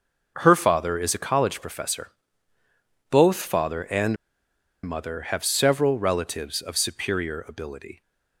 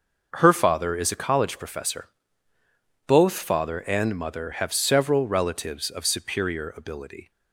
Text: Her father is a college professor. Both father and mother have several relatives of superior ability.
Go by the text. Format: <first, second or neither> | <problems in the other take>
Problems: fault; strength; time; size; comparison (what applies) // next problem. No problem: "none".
second | starts louder than the rest; noticeable; until 1.3 s; 6 dB; noticeable in the second // pauses between "and" and "mother"; noticeable; at 4.1 s; 0.69 s long